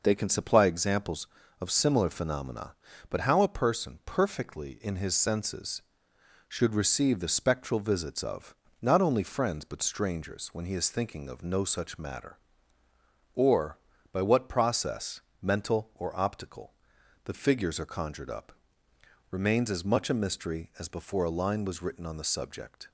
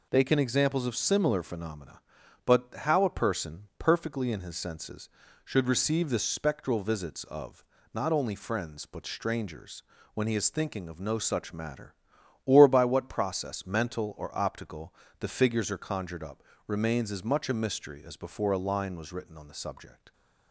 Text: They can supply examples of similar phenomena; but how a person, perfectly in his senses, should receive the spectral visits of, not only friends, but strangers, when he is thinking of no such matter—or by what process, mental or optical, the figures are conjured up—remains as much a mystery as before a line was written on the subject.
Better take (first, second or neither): first